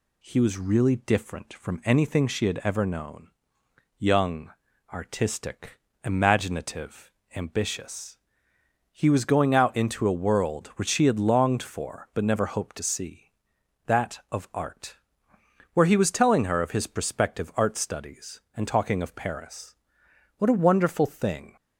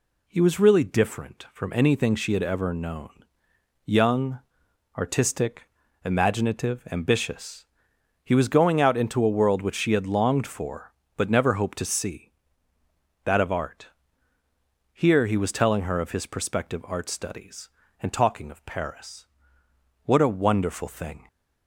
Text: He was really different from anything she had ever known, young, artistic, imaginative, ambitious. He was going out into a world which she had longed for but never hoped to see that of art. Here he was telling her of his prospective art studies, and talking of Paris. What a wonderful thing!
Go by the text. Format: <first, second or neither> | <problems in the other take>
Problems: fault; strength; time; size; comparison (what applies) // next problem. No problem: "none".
second | says "Where" for "Here"; at 15.7 s